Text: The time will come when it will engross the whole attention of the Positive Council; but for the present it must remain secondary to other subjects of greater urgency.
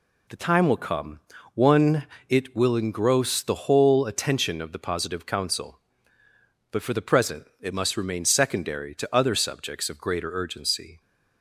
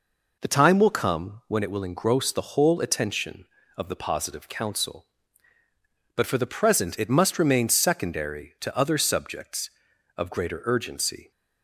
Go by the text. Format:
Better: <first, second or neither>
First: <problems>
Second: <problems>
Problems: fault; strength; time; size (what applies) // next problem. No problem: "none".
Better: second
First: says "one" for "when"; at 1.5 s // pauses between "present" and "it"; slight; at 7.4 s; 0.16 s long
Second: none